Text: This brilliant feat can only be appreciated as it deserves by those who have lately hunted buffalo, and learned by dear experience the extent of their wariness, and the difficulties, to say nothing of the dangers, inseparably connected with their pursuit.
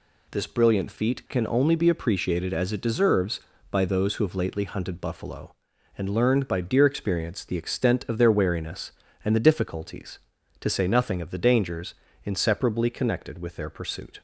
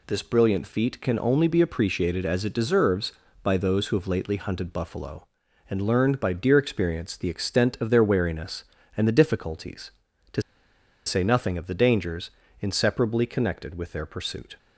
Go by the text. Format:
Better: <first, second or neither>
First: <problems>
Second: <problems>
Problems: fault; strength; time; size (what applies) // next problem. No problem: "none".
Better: first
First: none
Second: pauses between "to" and "say"; noticeable; at 10.4 s; 0.64 s long